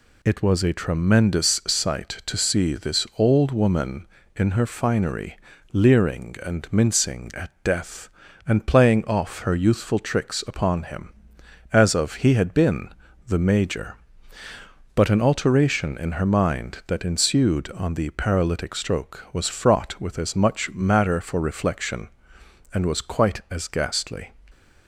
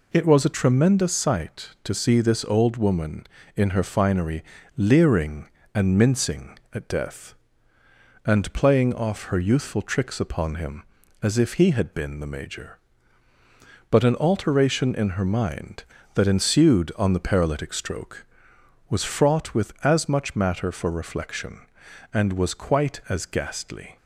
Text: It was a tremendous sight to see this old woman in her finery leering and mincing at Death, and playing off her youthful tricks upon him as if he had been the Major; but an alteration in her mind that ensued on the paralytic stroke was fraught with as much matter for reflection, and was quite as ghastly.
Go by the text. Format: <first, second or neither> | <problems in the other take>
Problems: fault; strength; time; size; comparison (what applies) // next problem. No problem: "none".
second | pauses between "finery" and "leering"; slight; at 5.3 s; 0.36 s long; slight in the second // says "of" for "if"; at 11.9 s // pauses between "been" and "the"; at 12.8 s; 0.40 s long